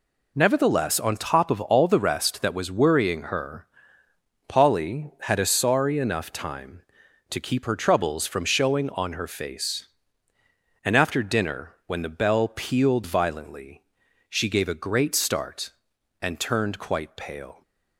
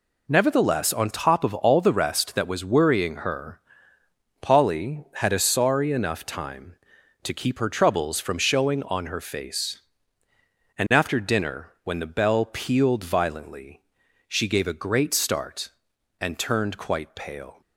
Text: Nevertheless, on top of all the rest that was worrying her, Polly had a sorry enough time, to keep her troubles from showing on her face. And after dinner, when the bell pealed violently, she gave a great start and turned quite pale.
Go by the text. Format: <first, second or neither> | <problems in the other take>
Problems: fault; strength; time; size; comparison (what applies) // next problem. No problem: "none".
neither | none